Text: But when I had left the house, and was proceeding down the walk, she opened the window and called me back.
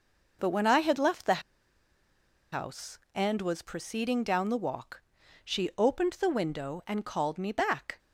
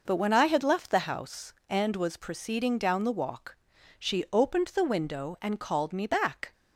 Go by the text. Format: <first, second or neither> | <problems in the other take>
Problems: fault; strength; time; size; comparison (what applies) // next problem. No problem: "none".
second | pauses between "the" and "house"; at 1.4 s; 1.1 s long